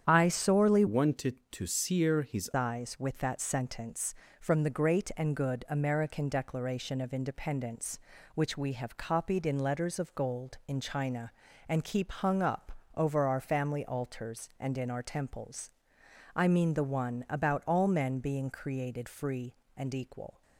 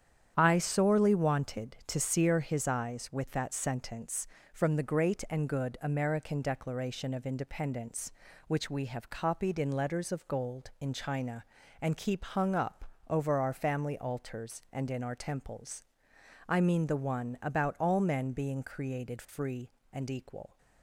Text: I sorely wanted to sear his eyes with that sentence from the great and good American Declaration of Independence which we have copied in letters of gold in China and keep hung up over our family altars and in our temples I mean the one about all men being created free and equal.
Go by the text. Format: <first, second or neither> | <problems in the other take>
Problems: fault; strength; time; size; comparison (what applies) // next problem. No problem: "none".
second | starts louder than the rest; strong; until 1.0 s; 9 dB; strong in the second // changes voice from "wanted" to "his"; from 0.8 to 2.4 s; 1.6 s long // pauses between "up" and "over"; slight; at 12.7 s; 0.24 s long; slight in the second // pauses between "temples" and "I"; noticeable; at 15.7 s; 0.64 s long; noticeable in the second